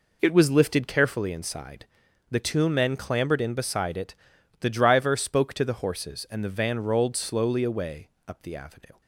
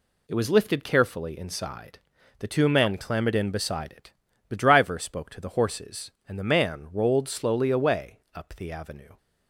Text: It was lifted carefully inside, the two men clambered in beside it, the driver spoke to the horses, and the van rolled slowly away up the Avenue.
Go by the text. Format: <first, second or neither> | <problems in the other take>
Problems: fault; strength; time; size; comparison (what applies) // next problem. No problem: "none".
first | says "man" for "van"; at 6.4 s // pauses between "away" and "up"; slight; at 8.1 s; 0.16 s long; slight in the first